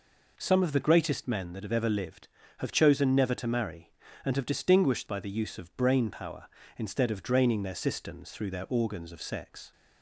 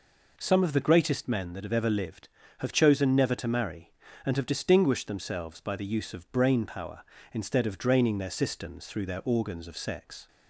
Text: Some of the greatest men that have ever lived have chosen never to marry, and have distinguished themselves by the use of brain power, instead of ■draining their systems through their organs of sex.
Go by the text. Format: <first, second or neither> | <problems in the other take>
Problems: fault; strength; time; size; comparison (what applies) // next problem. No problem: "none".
second | skips "themselves"; at 5.0 s